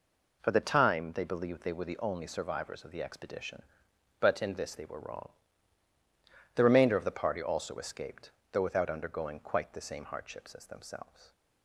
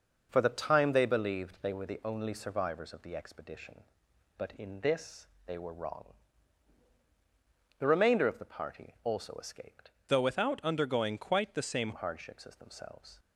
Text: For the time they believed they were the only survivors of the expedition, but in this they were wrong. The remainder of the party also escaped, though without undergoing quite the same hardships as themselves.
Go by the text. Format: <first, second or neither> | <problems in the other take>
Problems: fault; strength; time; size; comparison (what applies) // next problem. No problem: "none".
first | pauses between "this" and "they"; slight; at 5.2 s; 0.20 s long // changes voice from "though" to "same"; from 10.0 to 11.9 s; 1.9 s long